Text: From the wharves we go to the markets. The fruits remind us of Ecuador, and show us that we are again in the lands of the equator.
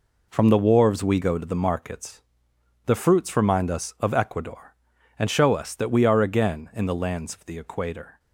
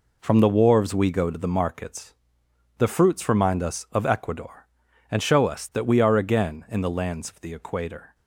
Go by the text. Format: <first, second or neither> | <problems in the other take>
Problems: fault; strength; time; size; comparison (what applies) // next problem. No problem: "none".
neither | none